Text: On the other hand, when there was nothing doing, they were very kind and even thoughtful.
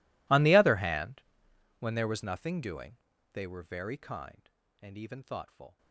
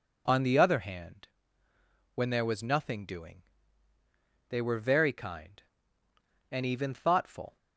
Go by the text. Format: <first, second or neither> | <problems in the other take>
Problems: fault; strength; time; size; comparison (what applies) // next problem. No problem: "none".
second | gets quieter; strong; throughout; 26.5 dB